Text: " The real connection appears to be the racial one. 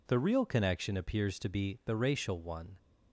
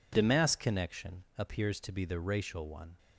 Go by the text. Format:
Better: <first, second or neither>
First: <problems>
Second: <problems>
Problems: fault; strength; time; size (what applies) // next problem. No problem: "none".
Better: first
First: none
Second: says "mass" for "real"; at 0.2 s